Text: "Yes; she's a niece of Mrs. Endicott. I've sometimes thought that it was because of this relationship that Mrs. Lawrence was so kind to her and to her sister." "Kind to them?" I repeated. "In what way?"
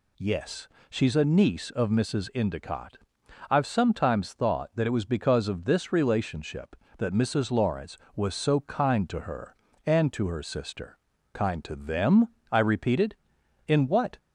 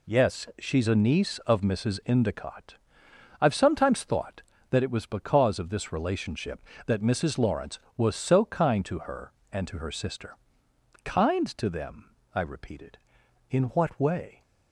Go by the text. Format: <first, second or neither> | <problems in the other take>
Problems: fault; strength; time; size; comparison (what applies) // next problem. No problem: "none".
second | stops before "way"; at 14.1 s